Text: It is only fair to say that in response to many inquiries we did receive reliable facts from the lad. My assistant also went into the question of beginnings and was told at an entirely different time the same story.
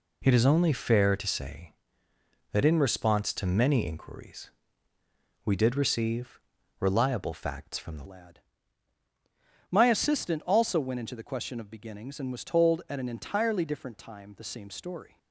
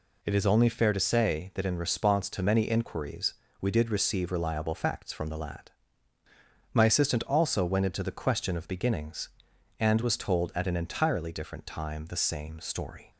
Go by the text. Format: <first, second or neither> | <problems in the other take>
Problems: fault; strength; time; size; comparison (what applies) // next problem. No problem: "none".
second | pauses between "inquiries" and "we"; noticeable; at 4.5 s; 0.94 s long; slight in the second // pauses between "receive" and "reliable"; at 6.3 s; 0.40 s long // changes voice at "lad"; from 8.0 s on; 7.1 s long